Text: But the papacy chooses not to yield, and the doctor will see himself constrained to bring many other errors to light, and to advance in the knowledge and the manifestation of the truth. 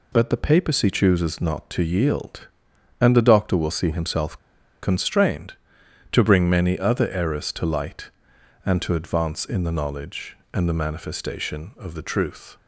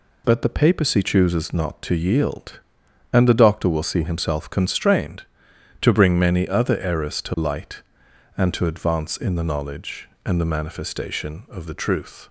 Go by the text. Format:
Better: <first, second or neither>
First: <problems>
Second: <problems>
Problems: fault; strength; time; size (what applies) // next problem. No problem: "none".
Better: second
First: pauses between "himself" and "constrained"; at 4.3 s; 0.45 s long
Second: none